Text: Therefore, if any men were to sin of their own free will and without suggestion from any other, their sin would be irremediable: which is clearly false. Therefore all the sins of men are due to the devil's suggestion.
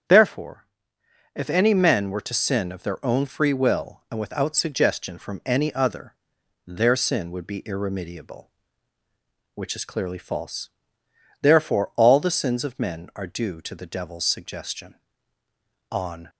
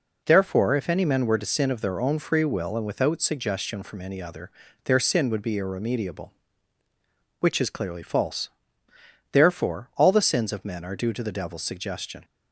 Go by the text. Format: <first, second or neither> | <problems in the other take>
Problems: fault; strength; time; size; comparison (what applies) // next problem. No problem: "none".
second | starts louder than the rest; strong; until 1.7 s; 8 dB // goes on to say "On"; slight; from 15.9 s on; 0.38 s long